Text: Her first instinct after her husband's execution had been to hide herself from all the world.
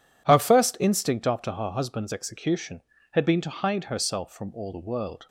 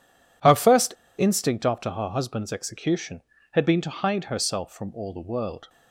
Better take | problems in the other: first | pauses between "first" and "instinct"; slight; at 0.9 s; 0.24 s long

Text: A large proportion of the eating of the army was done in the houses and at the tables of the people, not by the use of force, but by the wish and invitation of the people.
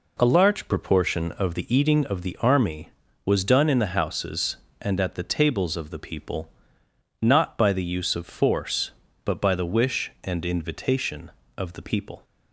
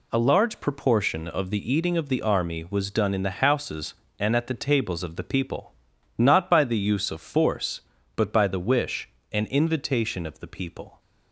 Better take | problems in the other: neither | none

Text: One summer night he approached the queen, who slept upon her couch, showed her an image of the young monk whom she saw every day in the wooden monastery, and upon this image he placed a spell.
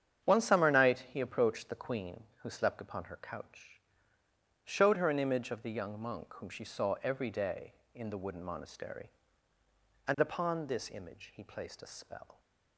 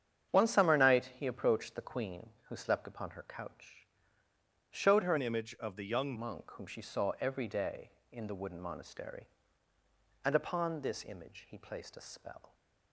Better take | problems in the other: first | starts louder than the rest; strong; until 1.4 s; 8.5 dB; strong in the first // changes voice from "an" to "young"; from 5.1 to 6.1 s; 1.0 s long

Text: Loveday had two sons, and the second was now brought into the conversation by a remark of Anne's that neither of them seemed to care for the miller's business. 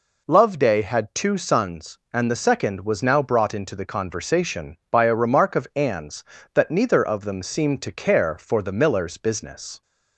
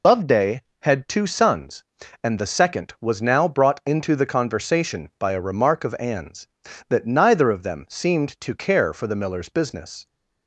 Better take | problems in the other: first | loses the start of "Loveday"; at 0.0 s; 70 ms

